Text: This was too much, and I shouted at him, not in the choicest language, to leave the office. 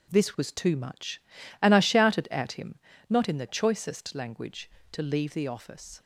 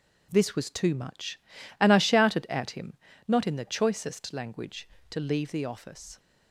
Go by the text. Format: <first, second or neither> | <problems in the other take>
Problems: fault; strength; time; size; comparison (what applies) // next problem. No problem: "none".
neither | none